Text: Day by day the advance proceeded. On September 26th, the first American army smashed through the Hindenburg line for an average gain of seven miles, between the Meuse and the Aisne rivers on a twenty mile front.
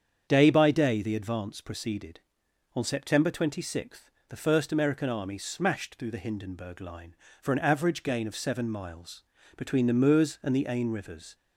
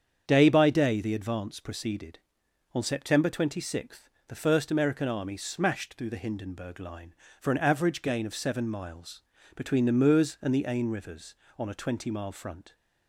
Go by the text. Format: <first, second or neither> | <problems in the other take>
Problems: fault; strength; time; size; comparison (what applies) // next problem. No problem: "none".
second | starts louder than the rest; strong; until 1.3 s; 7.5 dB; strong in the second // stops before "on a twenty mile front"; at 11.3 s